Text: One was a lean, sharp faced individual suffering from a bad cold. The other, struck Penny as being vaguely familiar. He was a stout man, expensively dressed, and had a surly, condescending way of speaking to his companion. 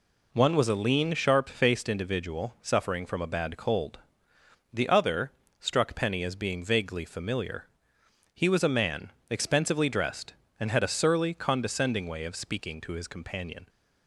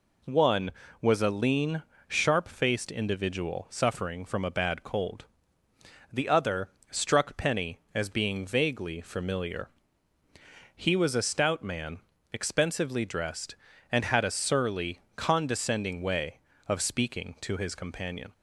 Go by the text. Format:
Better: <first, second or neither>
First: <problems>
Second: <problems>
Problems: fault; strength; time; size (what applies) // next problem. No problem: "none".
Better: second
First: skips "stout"; at 8.6 s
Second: none